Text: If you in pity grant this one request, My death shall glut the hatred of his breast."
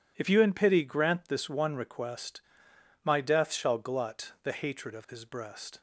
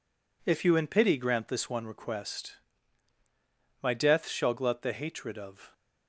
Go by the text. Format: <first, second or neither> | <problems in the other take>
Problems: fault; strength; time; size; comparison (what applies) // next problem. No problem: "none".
first | stops before "his breast"; at 5.7 s